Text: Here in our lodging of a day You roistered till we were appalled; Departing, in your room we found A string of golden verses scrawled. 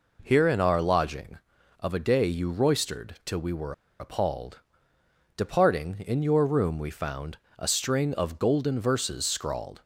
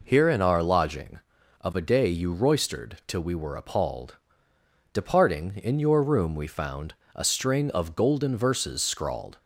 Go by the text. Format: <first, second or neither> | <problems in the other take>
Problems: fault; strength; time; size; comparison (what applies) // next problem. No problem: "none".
second | pauses between "were" and "appalled"; slight; at 3.7 s; 0.27 s long // pauses between "found" and "A"; slight; at 7.3 s; 0.20 s long; slight in the second